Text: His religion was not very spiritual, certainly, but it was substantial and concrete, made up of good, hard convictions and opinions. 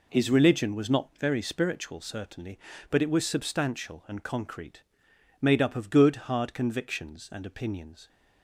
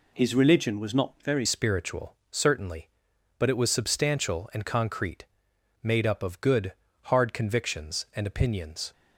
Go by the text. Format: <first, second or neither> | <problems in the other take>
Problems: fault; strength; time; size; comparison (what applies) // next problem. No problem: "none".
first | changes voice at "spiritual"; from 1.4 s on; 7.5 s long